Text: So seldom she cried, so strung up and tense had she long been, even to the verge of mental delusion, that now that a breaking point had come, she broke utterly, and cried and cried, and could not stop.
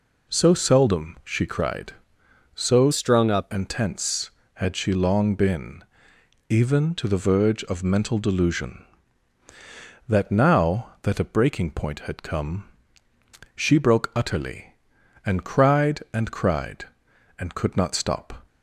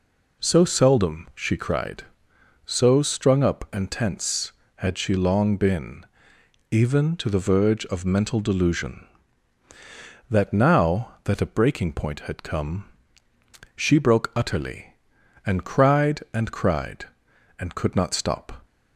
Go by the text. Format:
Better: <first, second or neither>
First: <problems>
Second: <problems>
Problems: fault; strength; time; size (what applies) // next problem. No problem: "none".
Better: second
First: changes voice from "strung" to "up"; from 2.9 to 3.4 s; 0.5 s long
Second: none